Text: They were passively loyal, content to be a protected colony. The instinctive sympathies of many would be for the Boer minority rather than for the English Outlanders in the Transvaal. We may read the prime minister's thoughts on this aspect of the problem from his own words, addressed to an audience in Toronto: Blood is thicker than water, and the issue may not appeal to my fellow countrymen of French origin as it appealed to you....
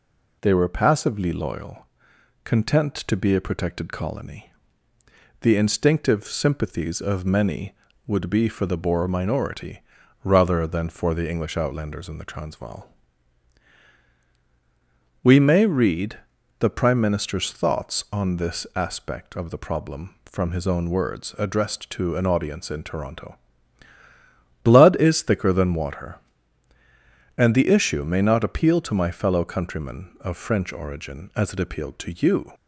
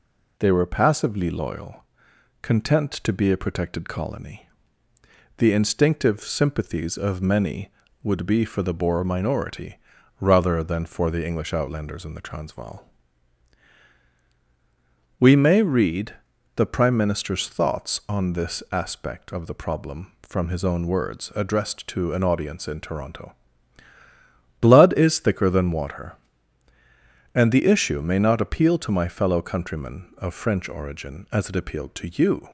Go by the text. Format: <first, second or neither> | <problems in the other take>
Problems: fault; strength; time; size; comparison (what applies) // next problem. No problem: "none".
neither | pauses between "minority" and "rather"; the same in both // pauses between "read" and "the"; the same in both